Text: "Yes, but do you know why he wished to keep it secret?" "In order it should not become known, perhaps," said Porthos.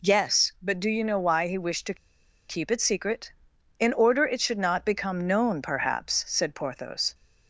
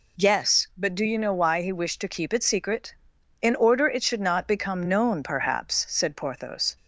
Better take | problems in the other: second | pauses between "to" and "keep"; noticeable; at 1.9 s; 0.55 s long

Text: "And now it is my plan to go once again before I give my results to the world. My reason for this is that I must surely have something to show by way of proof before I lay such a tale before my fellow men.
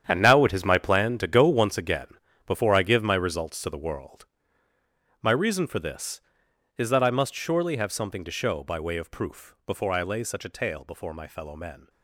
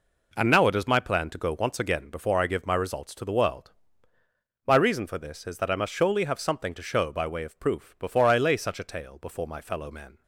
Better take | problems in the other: second | gets quieter; strong; throughout; 13 dB // pauses between "again" and "before"; at 2.0 s; 0.38 s long

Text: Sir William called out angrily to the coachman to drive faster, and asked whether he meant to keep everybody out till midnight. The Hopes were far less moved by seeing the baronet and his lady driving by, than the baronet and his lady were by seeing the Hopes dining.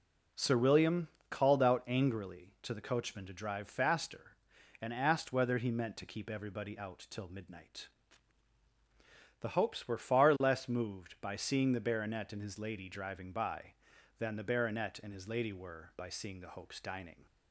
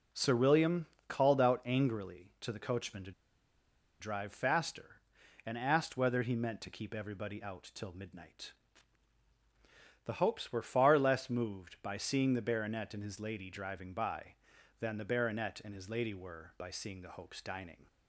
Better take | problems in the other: first | pauses between "William" and "called"; slight; at 0.8 s; 0.20 s long; slight in the first // pauses between "to" and "drive"; noticeable; at 3.1 s; 0.89 s long

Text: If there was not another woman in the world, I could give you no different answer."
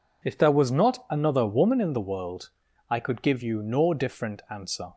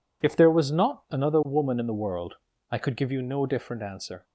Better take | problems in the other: neither | none

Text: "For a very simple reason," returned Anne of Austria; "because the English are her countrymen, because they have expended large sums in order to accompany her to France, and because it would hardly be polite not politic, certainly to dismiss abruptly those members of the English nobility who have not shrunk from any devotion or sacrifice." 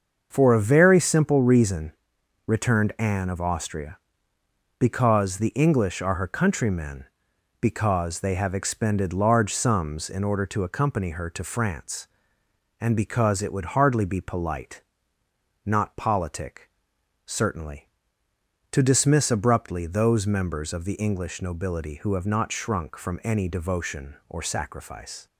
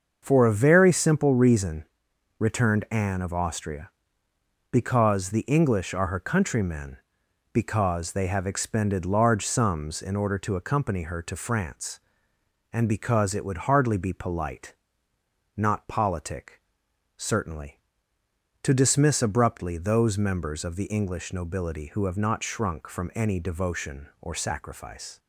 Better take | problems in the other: neither | starts louder than the rest; the same in both // pauses between "polite" and "not"; noticeable; the same in both

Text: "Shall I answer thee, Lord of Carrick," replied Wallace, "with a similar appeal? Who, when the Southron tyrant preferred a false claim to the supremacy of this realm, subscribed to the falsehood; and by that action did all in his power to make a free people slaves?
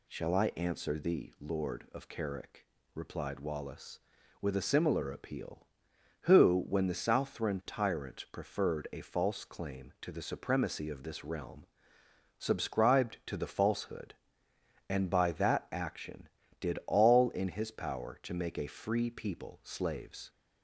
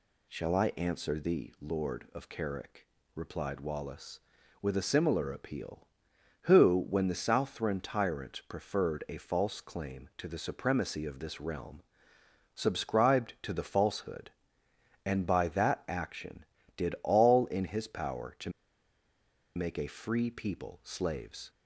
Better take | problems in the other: first | pauses between "to" and "make"; at 18.4 s; 1.0 s long

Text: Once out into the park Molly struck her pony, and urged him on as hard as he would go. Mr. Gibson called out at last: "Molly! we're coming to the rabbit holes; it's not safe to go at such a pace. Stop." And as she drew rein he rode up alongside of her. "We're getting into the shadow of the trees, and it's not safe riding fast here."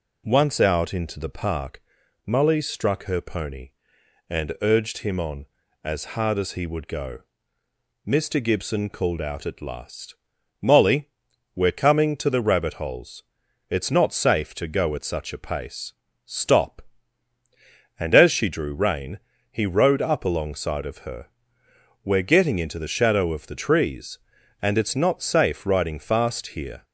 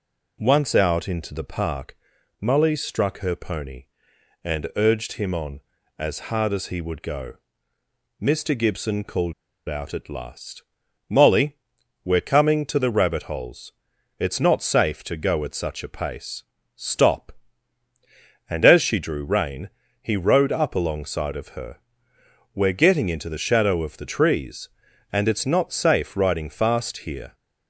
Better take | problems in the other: first | pauses between "park" and "Molly"; at 1.9 s; 0.42 s long; also in the first // pauses between "called" and "out"; slight; at 9.3 s; 0.34 s long // pauses between "rein" and "he"; slight; at 19.6 s; 0.32 s long; slight in the first

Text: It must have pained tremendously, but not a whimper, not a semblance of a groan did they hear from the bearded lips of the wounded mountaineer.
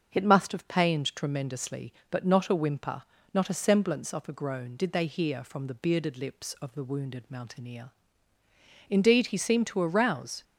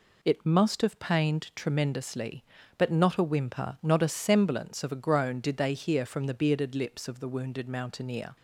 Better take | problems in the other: second | starts louder than the rest; until 1.1 s; 6.5 dB // goes on to say "Indeed he seemed to arouse"; from 8.8 s on; 1.5 s long

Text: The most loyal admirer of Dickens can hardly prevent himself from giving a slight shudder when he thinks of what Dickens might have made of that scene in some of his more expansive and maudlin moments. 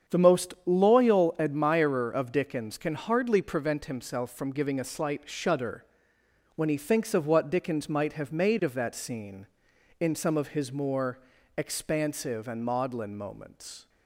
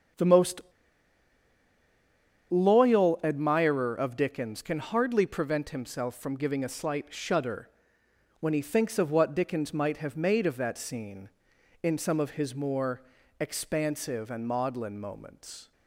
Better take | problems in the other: first | starts louder than the rest; strong; until 3.0 s; 8 dB; strong in the first // pauses between "most" and "loyal"; strong; at 0.5 s; 1.8 s long // pauses between "shudder" and "when"; noticeable; at 7.6 s; 0.72 s long; noticeable in the first // pauses between "more" and "expansive"; at 13.0 s; 0.38 s long; also in the first

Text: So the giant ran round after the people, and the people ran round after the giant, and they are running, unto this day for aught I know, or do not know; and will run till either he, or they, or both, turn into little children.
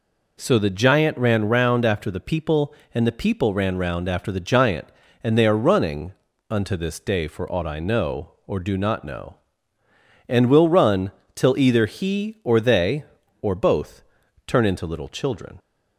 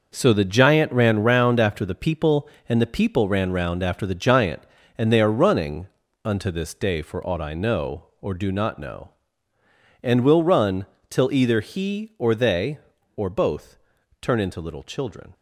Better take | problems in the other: first | gets quieter; strong; throughout; 9 dB // pauses between "run" and "till"; slight; at 10.8 s; 0.24 s long; slight in the first

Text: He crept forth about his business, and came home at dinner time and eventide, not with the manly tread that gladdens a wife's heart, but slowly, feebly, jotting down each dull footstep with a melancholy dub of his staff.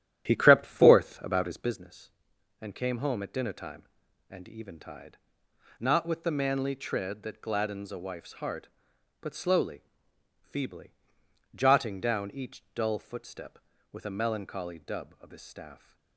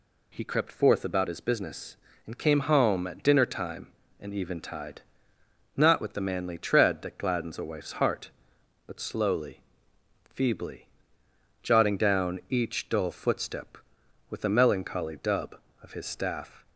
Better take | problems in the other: second | starts louder than the rest; strong; until 1.8 s; 11 dB

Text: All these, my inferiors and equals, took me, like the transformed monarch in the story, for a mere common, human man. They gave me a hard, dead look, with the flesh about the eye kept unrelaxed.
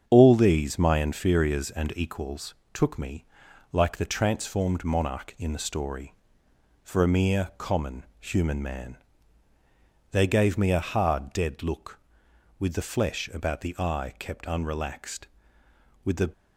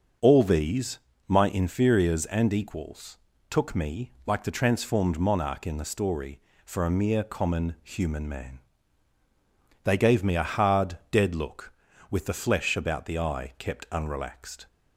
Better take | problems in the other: second | starts louder than the rest; strong; until 1.0 s; 7.5 dB; also in the second // goes on to say "With the"; slight; from 16.0 s on; 0.28 s long

